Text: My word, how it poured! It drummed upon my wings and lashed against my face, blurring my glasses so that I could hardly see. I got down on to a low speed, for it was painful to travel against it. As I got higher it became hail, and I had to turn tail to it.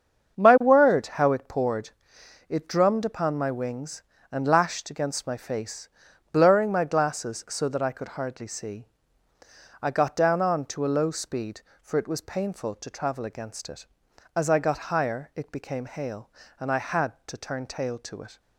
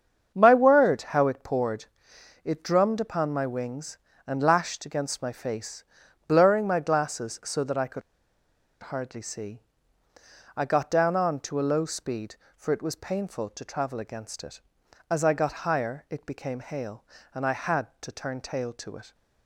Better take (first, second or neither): first